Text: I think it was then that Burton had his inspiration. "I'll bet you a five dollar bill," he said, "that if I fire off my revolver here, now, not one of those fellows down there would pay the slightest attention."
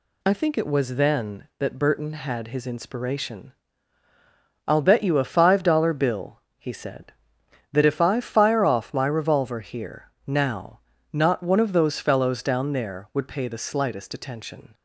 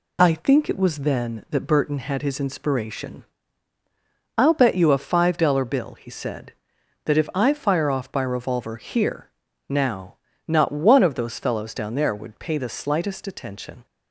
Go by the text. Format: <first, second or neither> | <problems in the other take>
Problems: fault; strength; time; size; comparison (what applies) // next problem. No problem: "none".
first | says "by" for "my"; at 8.1 s